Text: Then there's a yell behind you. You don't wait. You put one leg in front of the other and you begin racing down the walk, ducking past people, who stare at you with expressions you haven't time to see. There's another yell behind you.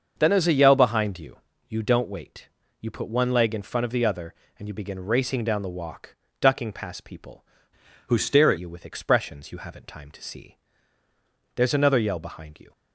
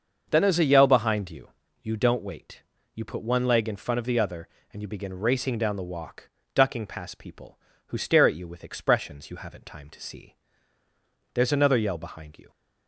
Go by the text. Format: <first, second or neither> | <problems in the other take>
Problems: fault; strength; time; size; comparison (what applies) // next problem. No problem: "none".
second | starts louder than the rest; until 1.1 s; 6.5 dB; also in the second // changes voice from "who" to "at"; from 8.0 to 8.5 s; 0.5 s long